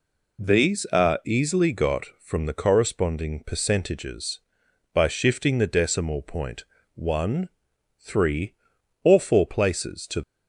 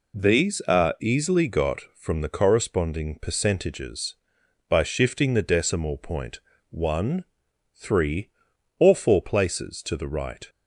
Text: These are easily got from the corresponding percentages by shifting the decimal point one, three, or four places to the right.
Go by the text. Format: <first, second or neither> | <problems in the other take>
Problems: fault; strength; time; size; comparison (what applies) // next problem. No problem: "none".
second | pauses between "point" and "one"; slight; at 6.6 s; 0.30 s long; slight in the second // stops before "the right"; at 10.2 s